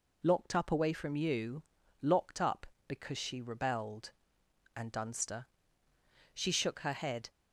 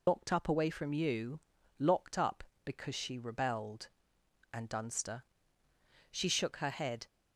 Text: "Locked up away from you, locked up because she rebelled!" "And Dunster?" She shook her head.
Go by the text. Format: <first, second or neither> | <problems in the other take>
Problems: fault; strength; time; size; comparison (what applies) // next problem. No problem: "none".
first | loses the start of "Locked"; at 0.0 s; 65 ms